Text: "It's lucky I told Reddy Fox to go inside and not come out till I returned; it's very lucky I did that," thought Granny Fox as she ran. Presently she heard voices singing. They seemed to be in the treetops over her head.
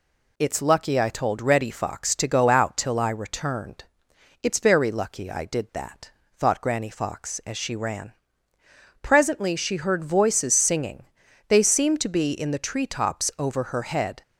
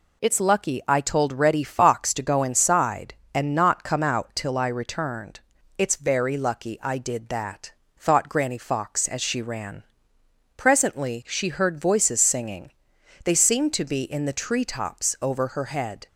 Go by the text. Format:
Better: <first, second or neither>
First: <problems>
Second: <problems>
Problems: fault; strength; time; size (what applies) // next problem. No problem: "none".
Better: second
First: skips "inside and not come"; at 2.4 s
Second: none